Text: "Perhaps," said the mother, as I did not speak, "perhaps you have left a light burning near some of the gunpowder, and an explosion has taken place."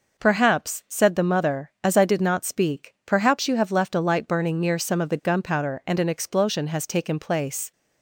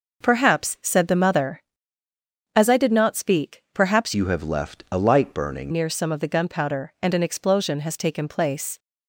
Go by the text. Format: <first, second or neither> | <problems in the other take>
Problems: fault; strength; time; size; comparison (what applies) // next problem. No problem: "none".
first | changes voice from "you" to "burning"; from 4.1 to 5.7 s; 1.6 s long